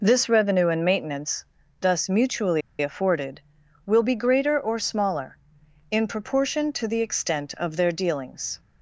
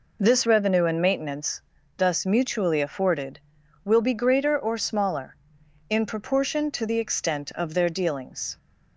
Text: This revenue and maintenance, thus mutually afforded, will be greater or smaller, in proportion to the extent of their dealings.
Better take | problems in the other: second | pauses between "mutually" and "afforded"; slight; at 2.6 s; 0.20 s long

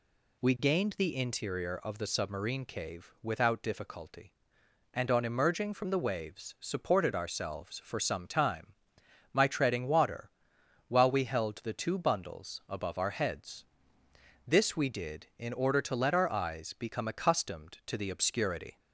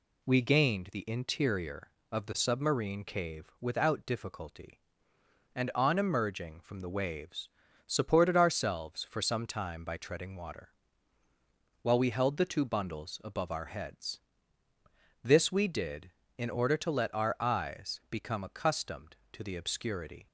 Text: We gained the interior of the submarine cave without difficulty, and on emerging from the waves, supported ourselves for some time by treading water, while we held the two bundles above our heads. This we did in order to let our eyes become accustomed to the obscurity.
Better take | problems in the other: second | says "my" for "by"; at 9.3 s

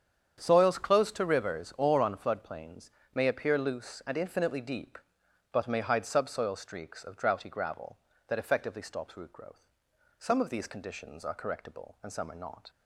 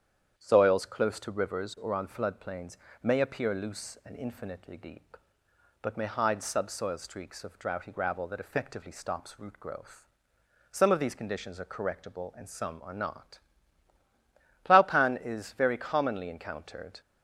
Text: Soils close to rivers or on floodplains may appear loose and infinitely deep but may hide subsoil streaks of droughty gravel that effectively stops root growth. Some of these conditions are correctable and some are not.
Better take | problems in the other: first | starts louder than the rest; strong; until 1.4 s; 8.5 dB; strong in the first // pauses between "floodplains" and "may"; slight; at 2.7 s; 0.26 s long; slight in the first // goes on to say "Plowpan is very commonly encountered"; strong; from 14.6 s on; 2.3 s long

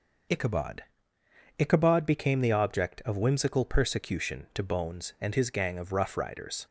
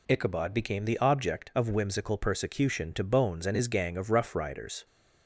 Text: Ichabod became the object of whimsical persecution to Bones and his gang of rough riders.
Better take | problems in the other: second | says "Ichabod" twice; at 1.5 s

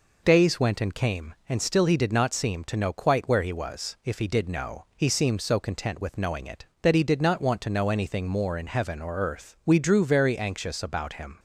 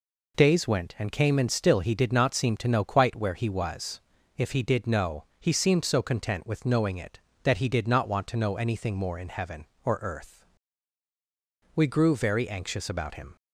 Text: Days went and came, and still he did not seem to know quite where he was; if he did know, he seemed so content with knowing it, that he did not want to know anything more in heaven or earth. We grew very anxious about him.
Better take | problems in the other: second | says "drew" for "grew"; at 9.7 s

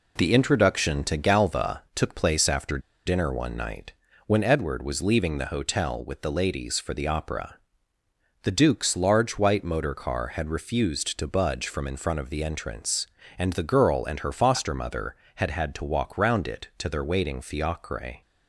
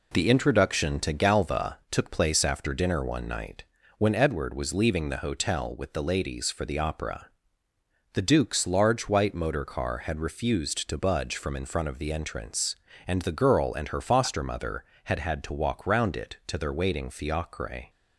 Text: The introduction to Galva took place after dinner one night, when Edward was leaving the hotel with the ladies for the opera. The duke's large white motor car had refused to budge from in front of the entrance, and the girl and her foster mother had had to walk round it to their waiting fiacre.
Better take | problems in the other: second | pauses between "after" and "dinner"; slight; at 2.7 s; 0.27 s long

